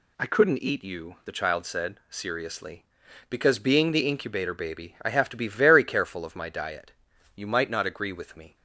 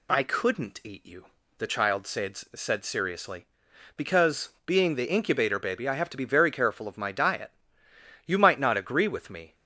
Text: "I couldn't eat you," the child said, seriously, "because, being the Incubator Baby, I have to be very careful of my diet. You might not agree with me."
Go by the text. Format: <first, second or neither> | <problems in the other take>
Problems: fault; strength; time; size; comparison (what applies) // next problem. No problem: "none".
first | says "said" twice; at 2.3 s